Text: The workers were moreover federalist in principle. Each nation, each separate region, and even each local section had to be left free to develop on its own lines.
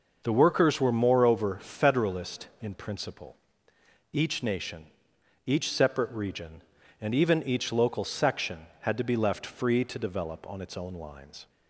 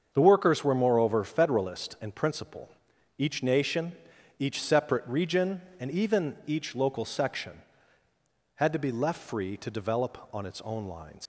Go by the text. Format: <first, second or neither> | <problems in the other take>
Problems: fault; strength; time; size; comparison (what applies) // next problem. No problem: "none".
first | starts louder than the rest; until 1.1 s; 7 dB // leaves "lines" unfinished; at 11.2 s; 115 ms